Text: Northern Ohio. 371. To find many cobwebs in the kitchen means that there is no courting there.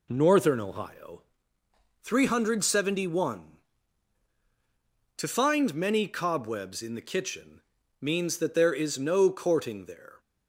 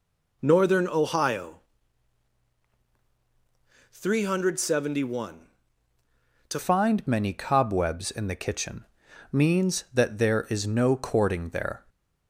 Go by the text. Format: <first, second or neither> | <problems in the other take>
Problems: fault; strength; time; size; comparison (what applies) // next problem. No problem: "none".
first | changes voice at "find"; from 6.5 s on; 5.3 s long // pauses between "kitchen" and "means"; noticeable; at 8.8 s; 0.48 s long; also in the first // stays silent after the last word; slight; from 11.7 s on; 0.5 s long